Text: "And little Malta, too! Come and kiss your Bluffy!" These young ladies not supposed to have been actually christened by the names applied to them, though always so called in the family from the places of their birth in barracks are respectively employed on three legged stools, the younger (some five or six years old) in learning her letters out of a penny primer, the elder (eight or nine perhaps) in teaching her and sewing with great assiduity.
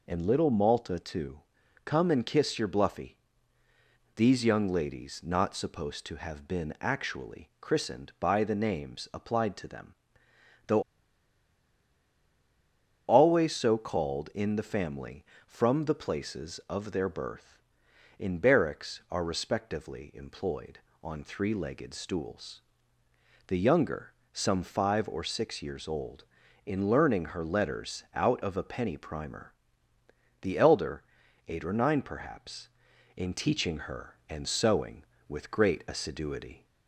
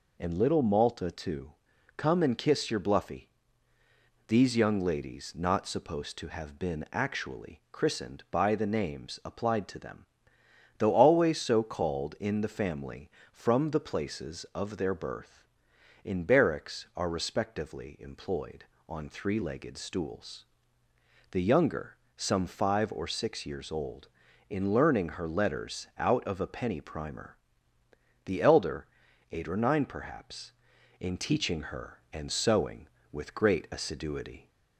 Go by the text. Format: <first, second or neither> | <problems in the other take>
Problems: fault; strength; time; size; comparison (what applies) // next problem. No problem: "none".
second | pauses between "though" and "always"; strong; at 10.8 s; 2.2 s long